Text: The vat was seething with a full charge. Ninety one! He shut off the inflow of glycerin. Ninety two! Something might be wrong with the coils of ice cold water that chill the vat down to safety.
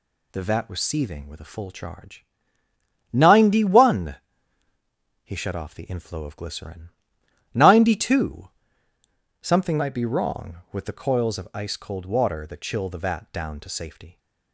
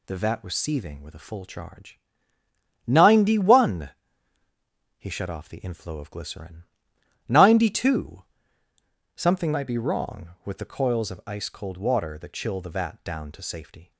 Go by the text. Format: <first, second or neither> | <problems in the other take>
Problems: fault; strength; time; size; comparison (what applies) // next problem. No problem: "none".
neither | none